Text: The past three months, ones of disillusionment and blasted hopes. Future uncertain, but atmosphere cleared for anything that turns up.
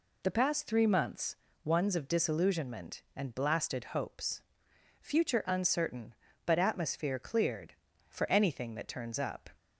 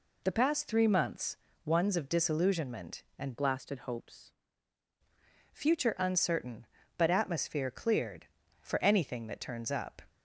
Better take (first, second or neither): first